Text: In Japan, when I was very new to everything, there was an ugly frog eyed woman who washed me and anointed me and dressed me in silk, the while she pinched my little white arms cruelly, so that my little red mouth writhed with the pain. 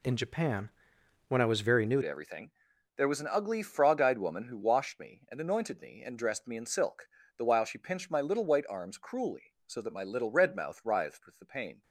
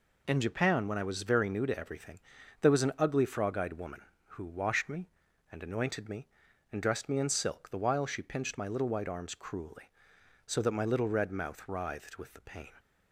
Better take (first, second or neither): second